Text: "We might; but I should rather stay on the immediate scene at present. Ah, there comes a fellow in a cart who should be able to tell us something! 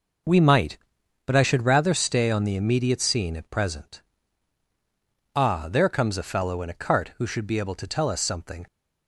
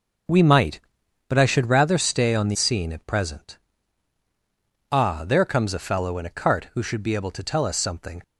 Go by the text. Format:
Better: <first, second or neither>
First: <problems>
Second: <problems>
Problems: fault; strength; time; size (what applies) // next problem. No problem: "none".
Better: first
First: none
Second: skips "immediate"; at 2.5 s